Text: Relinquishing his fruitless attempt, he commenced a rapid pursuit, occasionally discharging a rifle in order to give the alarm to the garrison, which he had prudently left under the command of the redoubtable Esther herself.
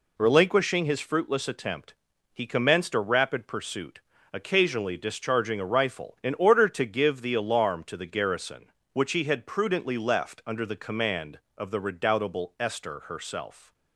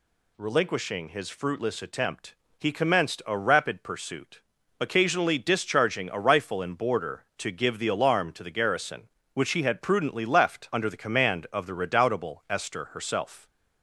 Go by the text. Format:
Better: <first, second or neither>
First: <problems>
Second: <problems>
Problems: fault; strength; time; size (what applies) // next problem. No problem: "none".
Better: first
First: none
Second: says "border" for "order"; at 6.7 s